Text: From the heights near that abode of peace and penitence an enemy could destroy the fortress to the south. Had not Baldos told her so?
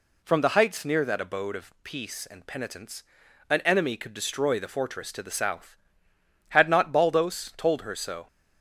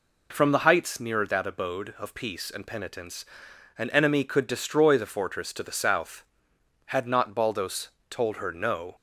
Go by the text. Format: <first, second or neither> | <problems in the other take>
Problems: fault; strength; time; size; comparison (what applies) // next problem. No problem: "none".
first | pauses between "penitence" and "an"; noticeable; at 3.2 s; 0.52 s long; noticeable in the first // pauses between "Baldos" and "told"; slight; at 7.8 s; 0.20 s long // says "no" for "so"; at 8.5 s